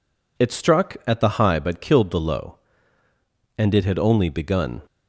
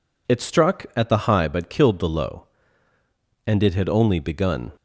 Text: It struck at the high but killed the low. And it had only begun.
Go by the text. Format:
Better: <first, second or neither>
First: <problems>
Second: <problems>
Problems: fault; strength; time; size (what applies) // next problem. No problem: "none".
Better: neither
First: none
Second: none